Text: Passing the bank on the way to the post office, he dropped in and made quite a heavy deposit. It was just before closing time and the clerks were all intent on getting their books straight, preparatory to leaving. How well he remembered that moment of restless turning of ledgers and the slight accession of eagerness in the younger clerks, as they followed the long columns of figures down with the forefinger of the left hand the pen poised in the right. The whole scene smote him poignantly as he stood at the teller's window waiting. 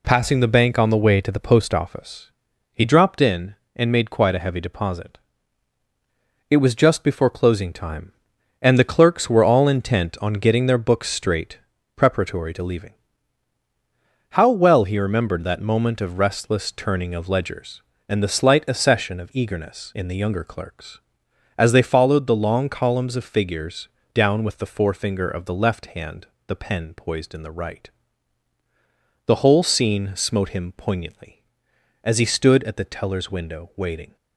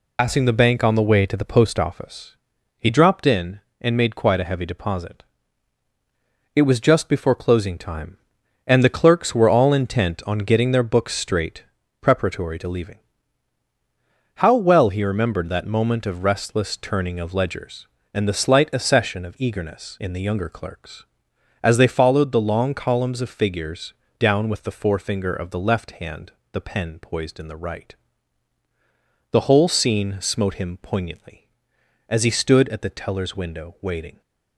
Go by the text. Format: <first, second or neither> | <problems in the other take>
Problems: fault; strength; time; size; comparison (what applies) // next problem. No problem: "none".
first | loses the start of "Passing"; at 0.1 s; 95 ms // pauses between "figures" and "down"; slight; at 23.9 s; 0.26 s long; slight in the first // pauses between "hand" and "the"; slight; at 26.3 s; 0.18 s long; slight in the first